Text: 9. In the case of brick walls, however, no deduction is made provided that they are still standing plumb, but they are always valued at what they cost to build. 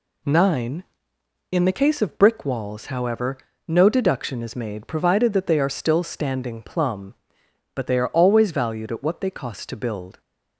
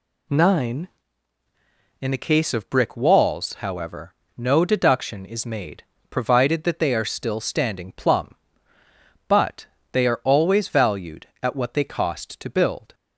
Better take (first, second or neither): first